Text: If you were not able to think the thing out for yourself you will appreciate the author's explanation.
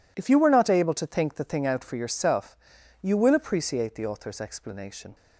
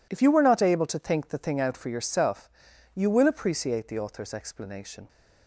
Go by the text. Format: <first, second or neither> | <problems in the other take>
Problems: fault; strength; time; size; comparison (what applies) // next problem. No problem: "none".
neither | pauses between "yourself" and "you"; noticeable; the same in both